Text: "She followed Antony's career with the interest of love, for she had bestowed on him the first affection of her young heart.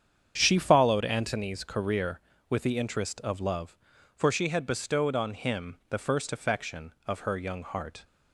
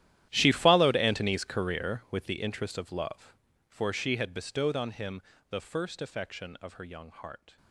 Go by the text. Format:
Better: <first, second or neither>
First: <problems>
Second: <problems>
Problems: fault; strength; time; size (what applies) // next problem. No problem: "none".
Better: first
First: starts louder than the rest; strong; until 1.3 s; 8 dB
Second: gets quieter; strong; throughout; 20.5 dB // starts louder than the rest; strong; until 1.3 s; 12.5 dB // pauses between "him" and "the"; slight; at 5.2 s; 0.26 s long